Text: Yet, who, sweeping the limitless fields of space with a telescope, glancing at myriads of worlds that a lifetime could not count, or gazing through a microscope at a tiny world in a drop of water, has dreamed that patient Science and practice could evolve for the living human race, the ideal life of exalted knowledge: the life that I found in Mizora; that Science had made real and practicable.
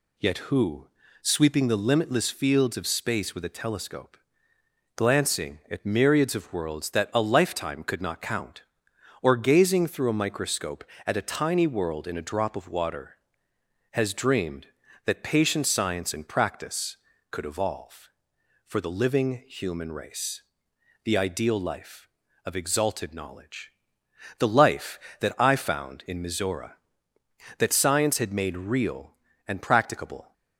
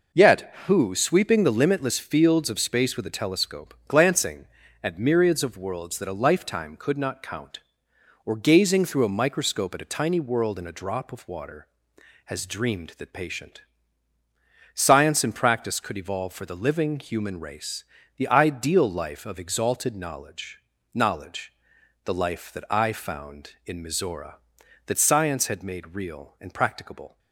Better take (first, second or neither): first